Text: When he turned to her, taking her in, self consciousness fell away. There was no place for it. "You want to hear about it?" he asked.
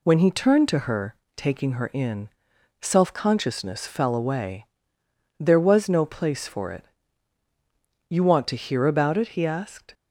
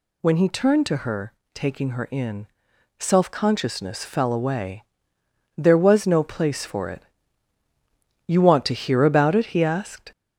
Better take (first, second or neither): first